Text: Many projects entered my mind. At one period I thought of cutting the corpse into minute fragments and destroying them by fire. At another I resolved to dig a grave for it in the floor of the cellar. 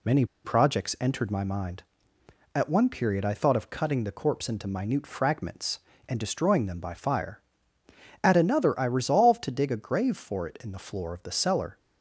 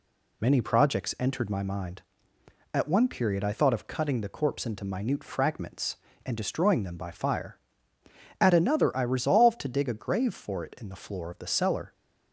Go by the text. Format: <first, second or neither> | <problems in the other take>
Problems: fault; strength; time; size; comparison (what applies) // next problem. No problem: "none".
second | pauses between "Many" and "projects"; slight; at 0.2 s; 0.20 s long